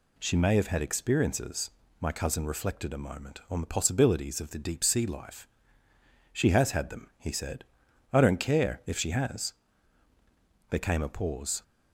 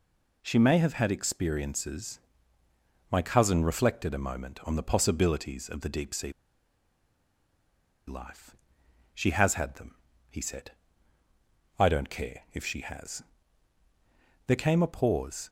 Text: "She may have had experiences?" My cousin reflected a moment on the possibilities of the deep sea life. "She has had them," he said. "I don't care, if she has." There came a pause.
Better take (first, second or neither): first